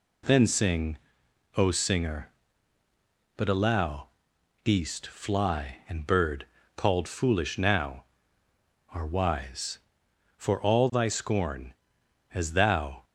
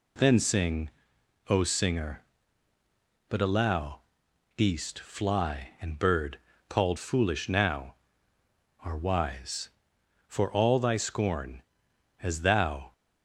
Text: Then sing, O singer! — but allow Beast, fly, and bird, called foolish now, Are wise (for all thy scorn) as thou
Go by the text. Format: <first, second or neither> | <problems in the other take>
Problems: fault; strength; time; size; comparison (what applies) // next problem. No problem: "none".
neither | pauses between "allow" and "Beast"; noticeable; the same in both